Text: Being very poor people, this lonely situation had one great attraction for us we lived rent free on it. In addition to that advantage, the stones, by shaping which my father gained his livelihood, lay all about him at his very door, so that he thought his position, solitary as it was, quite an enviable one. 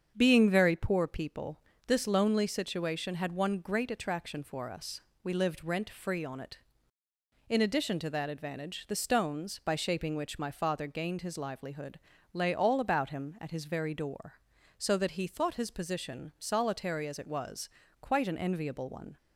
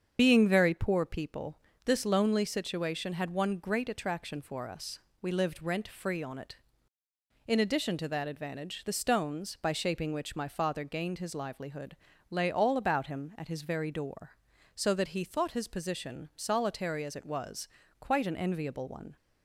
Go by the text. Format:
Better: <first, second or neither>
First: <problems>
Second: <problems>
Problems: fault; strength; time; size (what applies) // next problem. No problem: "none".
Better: first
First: starts louder than the rest; strong; until 1.1 s; 7.5 dB // pauses between "us" and "we"; slight; at 5.0 s; 0.24 s long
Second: loses the start of "Being"; at 0.1 s; 55 ms // starts louder than the rest; strong; until 1.2 s; 7.5 dB // pauses between "us" and "we"; slight; at 4.9 s; 0.24 s long